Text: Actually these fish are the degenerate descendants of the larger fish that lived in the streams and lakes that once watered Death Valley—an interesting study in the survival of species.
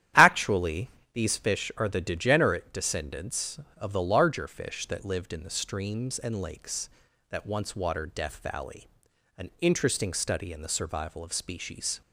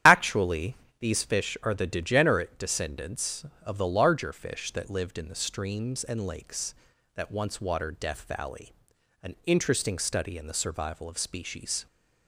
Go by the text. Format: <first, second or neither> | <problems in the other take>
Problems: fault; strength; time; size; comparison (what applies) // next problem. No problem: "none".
first | loses the start of "Actually"; at 0.0 s; 45 ms // starts louder than the rest; strong; until 1.3 s; 10.5 dB; strong in the first // pauses between "Actually" and "these"; slight; at 0.7 s; 0.24 s long; slight in the first